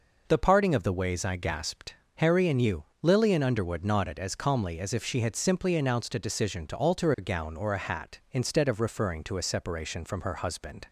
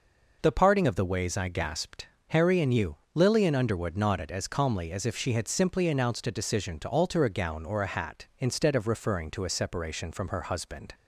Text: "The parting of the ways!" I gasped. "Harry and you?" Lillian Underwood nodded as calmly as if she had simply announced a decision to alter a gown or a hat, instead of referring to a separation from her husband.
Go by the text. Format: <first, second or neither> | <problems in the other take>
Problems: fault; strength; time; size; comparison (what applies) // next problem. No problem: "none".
neither | none